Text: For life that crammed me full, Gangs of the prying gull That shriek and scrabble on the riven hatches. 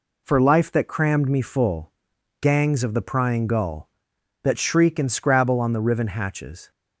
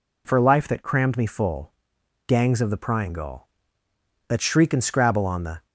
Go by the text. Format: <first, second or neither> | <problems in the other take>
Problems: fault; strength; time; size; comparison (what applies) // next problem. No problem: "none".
first | stops before "riven hatches"; at 5.6 s